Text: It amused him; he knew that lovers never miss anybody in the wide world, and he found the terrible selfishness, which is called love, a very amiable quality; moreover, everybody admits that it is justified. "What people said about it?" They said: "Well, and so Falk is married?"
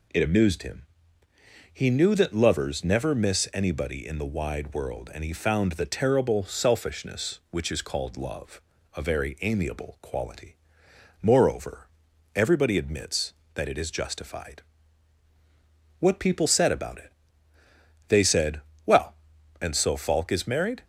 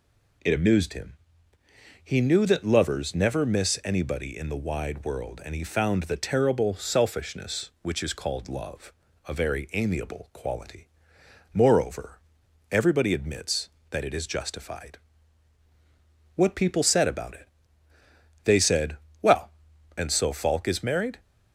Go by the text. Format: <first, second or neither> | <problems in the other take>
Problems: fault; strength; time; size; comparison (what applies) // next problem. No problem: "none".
neither | none